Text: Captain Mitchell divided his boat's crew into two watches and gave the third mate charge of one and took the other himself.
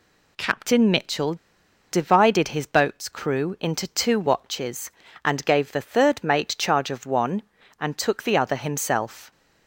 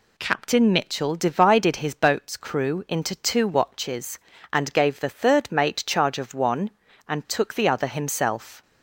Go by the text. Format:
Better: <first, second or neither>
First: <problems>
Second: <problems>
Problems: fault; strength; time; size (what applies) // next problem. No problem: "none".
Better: second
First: pauses between "Mitchell" and "divided"; noticeable; at 1.3 s; 0.56 s long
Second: none